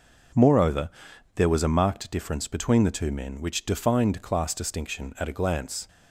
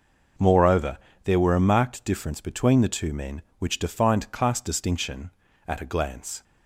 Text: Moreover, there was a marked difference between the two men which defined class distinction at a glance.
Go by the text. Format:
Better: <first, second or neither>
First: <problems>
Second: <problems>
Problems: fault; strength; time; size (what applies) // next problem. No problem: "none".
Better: first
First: none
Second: says "were" for "was"; at 1.3 s